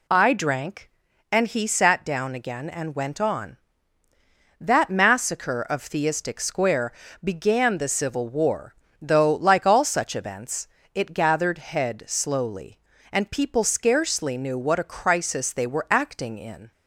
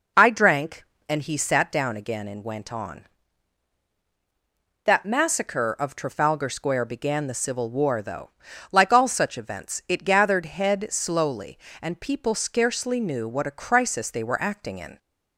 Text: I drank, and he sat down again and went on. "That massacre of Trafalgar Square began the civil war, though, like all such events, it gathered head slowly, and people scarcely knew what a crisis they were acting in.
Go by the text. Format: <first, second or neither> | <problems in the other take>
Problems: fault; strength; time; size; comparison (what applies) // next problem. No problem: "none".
second | says "Theistic" for "Trafalgar"; at 5.8 s // pauses between "Square" and "began"; slight; at 6.9 s; 0.28 s long